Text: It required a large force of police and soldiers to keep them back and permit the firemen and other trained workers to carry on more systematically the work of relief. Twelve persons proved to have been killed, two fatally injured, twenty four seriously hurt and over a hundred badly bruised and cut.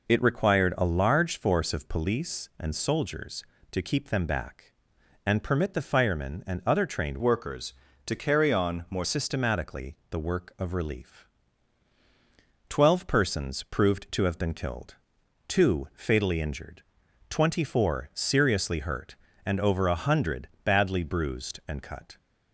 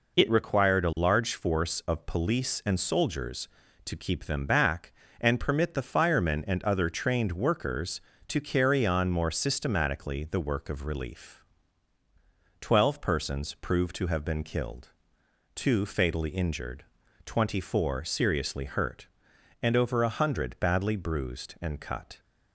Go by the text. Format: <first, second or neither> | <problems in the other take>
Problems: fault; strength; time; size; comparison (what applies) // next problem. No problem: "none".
second | changes voice from "workers" to "more"; from 7.1 to 9.0 s; 1.9 s long // pauses between "hundred" and "badly"; slight; at 20.4 s; 0.16 s long